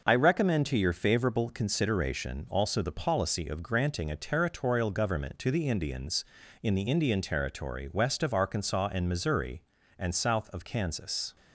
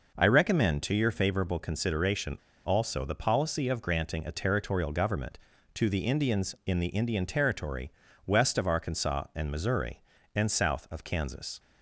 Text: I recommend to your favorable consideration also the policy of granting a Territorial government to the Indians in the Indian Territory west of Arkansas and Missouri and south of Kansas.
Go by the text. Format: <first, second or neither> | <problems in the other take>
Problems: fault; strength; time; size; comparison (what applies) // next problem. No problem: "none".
first | pauses between "consideration" and "also"; slight; at 2.3 s; 0.27 s long // pauses between "Territory" and "west"; slight; at 7.9 s; 0.36 s long